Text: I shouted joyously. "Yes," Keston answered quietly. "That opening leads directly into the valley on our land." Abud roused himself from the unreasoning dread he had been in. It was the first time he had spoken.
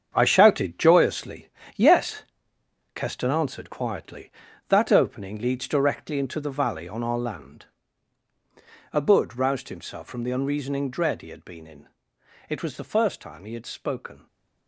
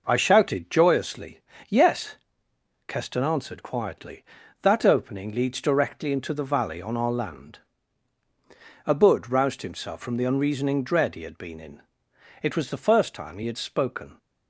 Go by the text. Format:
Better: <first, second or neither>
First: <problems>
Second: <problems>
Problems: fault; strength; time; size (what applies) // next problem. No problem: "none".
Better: second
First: gets quieter; strong; throughout; 11 dB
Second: none